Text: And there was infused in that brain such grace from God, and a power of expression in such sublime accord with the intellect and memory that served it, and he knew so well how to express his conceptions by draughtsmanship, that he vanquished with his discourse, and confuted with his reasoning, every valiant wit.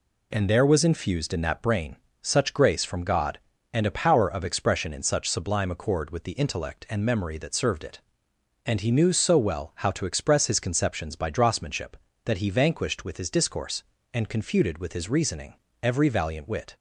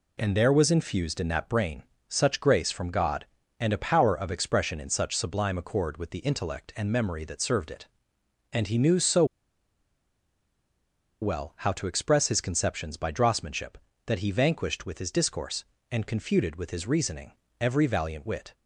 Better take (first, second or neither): first